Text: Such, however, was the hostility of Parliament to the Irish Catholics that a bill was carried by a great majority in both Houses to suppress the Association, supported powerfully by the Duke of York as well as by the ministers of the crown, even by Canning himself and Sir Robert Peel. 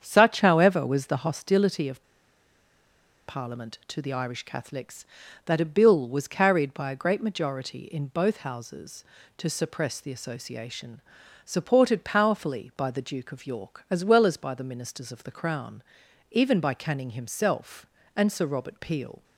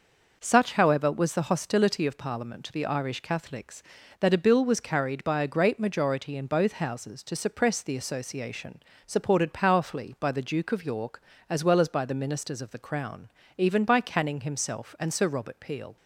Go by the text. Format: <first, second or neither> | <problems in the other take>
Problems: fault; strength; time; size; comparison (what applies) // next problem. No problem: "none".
second | starts louder than the rest; strong; until 1.0 s; 8 dB // pauses between "of" and "Parliament"; strong; at 2.0 s; 1.2 s long